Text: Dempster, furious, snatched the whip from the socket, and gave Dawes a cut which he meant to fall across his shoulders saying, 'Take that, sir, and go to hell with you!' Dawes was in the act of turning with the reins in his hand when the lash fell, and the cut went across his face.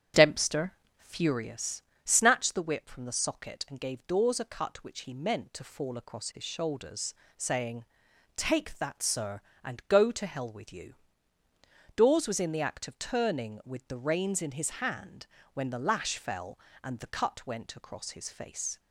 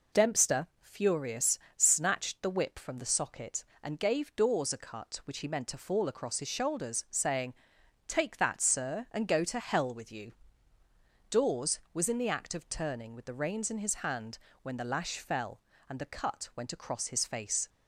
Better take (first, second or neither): second